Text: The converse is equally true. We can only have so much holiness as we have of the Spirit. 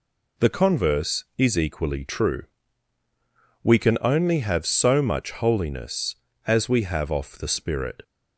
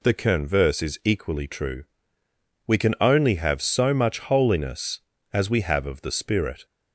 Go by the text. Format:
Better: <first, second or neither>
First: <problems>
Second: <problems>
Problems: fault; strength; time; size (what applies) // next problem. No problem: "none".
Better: second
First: says "off" for "of"; at 7.1 s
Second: none